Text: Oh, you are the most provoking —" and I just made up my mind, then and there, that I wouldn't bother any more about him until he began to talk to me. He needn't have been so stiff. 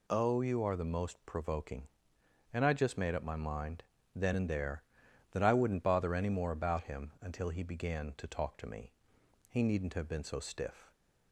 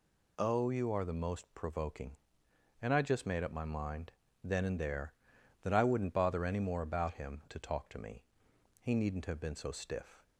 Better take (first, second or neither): first